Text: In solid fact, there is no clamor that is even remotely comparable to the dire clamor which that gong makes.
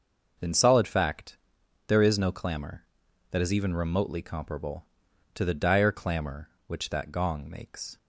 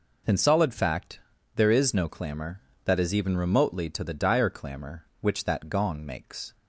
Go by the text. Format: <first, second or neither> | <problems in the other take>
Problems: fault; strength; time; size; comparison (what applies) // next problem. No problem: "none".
first | skips "comparable"; at 3.9 s